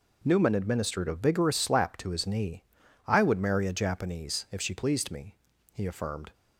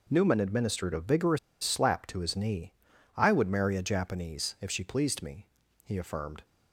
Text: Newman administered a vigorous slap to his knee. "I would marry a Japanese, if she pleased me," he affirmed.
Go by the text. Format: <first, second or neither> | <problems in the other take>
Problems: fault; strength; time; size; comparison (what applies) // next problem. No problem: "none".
first | pauses between "vigorous" and "slap"; slight; at 1.3 s; 0.25 s long